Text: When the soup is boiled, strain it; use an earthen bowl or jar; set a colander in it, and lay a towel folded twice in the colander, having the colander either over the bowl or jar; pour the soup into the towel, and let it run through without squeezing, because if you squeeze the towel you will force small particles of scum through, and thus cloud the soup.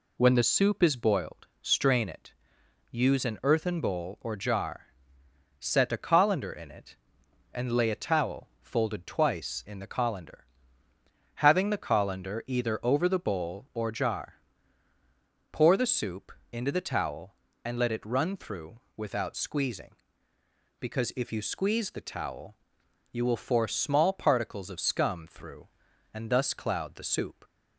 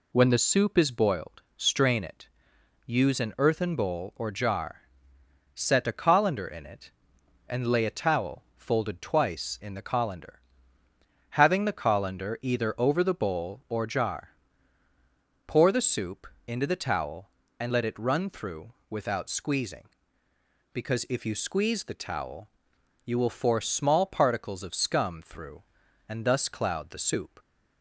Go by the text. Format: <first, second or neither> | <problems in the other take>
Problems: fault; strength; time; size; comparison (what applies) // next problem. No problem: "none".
neither | pauses between "soup" and "into"; slight; the same in both // pauses between "through" and "without"; slight; the same in both // pauses between "towel" and "you"; noticeable; the same in both